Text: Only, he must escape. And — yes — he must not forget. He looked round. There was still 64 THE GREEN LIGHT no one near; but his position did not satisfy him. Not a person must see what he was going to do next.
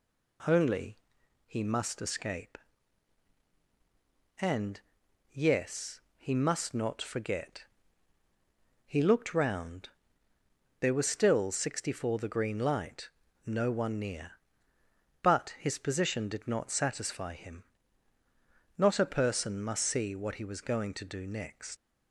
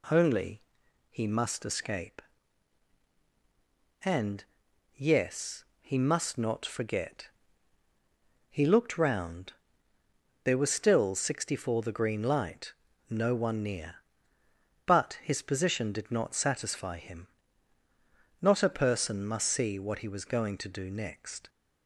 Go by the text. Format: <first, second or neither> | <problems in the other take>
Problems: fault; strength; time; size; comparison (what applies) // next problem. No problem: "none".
second | pauses between "LIGHT" and "no"; slight; at 13.0 s; 0.36 s long; slight in the second // leaves "next" unfinished; at 21.7 s; 85 ms